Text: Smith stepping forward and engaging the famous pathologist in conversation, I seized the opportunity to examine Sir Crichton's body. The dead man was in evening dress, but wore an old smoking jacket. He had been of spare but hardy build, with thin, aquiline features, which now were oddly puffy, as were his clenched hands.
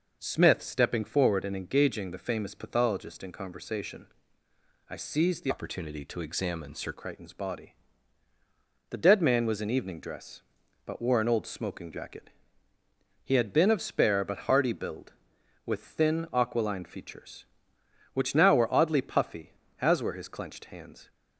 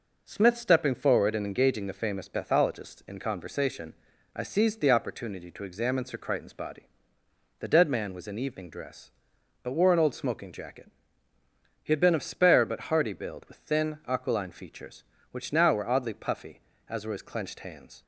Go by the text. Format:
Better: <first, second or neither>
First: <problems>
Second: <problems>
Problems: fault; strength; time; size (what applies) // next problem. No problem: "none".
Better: second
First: changes voice from "opportunity" to "Sir"; from 5.4 to 6.9 s; 1.5 s long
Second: none